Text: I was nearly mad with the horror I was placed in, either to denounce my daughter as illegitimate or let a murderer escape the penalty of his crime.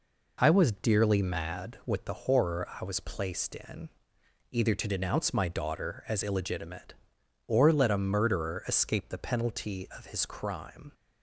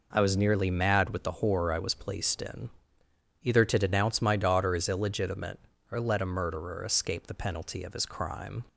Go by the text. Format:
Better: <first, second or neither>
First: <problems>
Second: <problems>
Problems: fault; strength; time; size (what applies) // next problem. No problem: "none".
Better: second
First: says "dearly" for "nearly"; at 0.7 s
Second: none